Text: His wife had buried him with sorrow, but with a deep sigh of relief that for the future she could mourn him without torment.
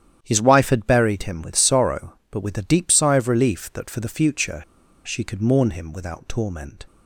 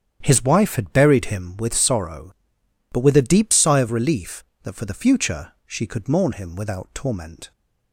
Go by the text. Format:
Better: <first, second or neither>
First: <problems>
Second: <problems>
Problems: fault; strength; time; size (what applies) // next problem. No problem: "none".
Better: second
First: starts louder than the rest; strong; until 1.2 s; 10 dB // pauses between "future" and "she"; at 4.6 s; 0.45 s long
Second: starts louder than the rest; strong; until 1.2 s; 9 dB